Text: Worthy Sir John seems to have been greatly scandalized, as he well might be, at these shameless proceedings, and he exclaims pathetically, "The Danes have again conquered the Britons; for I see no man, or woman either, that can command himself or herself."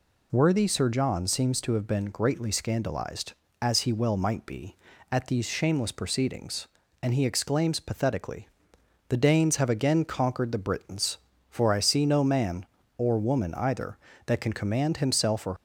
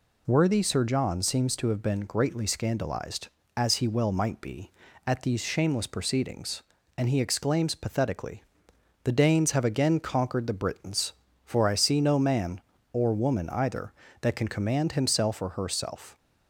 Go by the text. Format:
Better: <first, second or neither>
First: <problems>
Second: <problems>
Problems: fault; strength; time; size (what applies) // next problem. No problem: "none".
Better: second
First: stops before "herself"; at 15.5 s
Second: none